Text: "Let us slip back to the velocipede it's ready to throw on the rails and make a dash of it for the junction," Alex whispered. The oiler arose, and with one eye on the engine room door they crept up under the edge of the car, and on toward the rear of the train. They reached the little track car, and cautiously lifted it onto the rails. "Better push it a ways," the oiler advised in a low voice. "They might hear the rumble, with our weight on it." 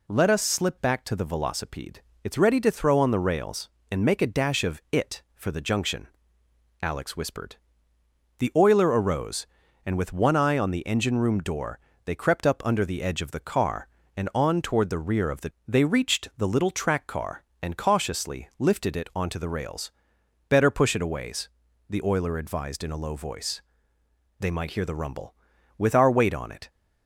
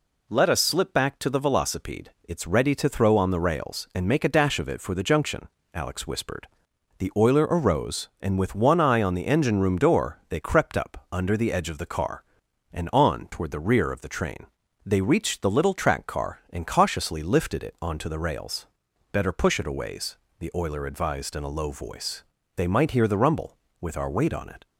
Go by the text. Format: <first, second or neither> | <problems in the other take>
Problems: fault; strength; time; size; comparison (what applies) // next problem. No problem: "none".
second | pauses between "velocipede" and "it's"; slight; at 1.9 s; 0.24 s long // pauses between "door" and "they"; slight; at 11.7 s; 0.28 s long // skips "train"; at 15.5 s